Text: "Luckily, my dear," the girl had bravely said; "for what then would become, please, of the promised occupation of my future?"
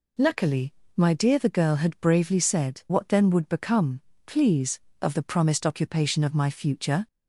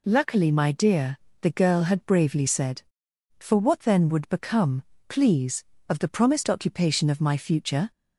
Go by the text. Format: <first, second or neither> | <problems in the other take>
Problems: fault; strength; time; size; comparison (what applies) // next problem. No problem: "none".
second | skips "for"; at 2.8 s